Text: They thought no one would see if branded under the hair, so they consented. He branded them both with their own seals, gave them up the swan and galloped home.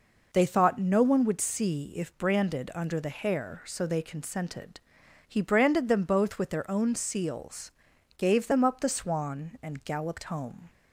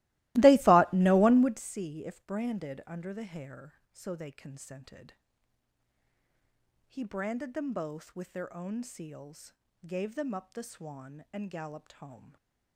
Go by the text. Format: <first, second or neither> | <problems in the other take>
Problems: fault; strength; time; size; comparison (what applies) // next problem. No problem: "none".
first | starts louder than the rest; strong; until 1.7 s; 19 dB